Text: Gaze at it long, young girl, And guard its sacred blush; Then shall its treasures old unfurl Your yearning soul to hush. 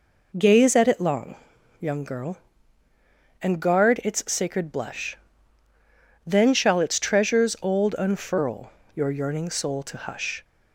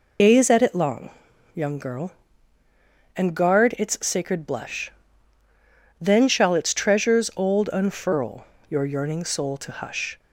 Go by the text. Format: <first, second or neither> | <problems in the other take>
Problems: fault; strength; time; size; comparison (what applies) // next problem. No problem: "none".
first | loses the start of "Gaze"; at 0.1 s; 115 ms // pauses between "unfurl" and "Your"; slight; at 8.4 s; 0.24 s long; slight in the first